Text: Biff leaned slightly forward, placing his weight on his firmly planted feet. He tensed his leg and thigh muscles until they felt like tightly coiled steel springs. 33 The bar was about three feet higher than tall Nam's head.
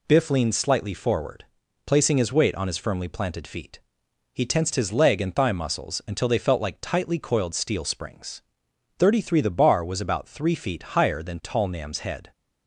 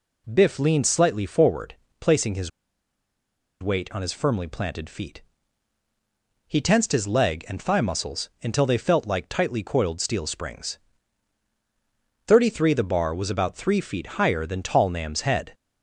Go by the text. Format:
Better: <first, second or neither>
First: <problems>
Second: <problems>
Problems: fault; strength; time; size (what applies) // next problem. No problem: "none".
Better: first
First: none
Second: pauses between "his" and "weight"; at 2.4 s; 1.1 s long